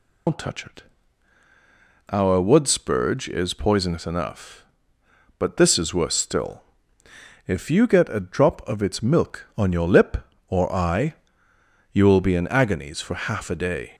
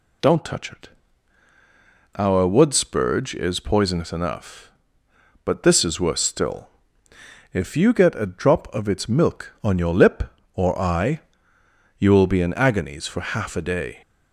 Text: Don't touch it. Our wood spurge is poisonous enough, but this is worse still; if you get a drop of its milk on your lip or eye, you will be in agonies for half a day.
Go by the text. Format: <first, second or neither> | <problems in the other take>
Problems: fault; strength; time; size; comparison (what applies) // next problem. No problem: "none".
second | loses the start of "Don't"; at 0.2 s; 115 ms